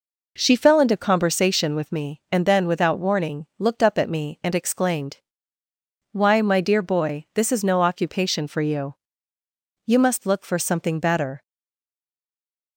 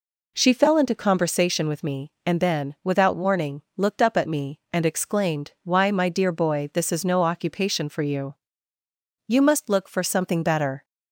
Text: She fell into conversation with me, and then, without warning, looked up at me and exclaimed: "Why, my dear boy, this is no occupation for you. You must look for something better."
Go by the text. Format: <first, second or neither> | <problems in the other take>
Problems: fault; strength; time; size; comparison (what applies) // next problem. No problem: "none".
second | stays silent after the last word; noticeable; from 11.4 s on; 1.3 s long